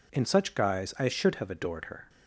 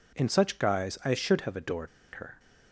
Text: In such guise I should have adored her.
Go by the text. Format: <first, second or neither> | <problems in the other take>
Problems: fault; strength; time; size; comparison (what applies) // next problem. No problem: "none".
first | pauses between "adored" and "her"; slight; at 1.8 s; 0.26 s long